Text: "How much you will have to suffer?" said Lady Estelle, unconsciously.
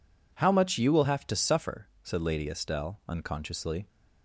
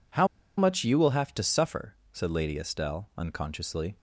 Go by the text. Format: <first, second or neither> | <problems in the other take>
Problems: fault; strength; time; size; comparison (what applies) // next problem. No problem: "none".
first | pauses between "How" and "much"; slight; at 0.2 s; 0.31 s long